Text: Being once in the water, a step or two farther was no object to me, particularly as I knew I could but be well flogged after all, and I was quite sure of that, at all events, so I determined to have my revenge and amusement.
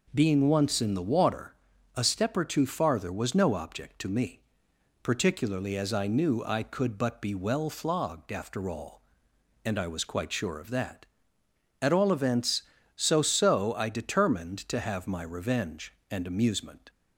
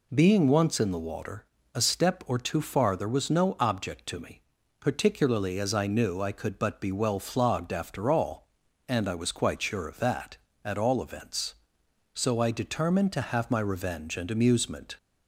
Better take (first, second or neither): second